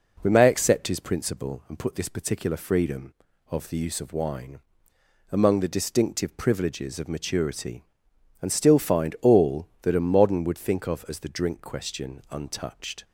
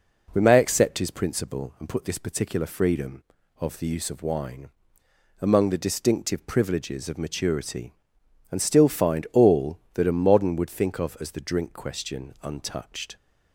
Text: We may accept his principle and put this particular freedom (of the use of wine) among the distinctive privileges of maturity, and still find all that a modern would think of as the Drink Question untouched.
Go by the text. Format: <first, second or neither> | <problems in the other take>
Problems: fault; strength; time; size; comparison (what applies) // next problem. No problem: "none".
neither | none